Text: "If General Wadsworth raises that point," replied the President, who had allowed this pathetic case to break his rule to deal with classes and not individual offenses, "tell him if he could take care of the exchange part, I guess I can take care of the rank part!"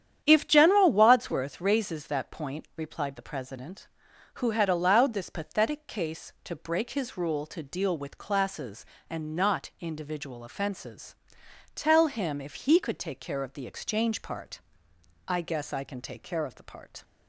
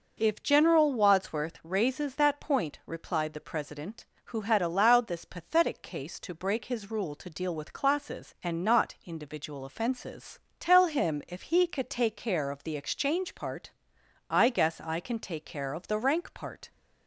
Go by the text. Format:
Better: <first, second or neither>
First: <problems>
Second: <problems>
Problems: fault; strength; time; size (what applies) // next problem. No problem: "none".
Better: second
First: starts louder than the rest; strong; until 1.2 s; 9.5 dB // skips "rank"; at 16.6 s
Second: none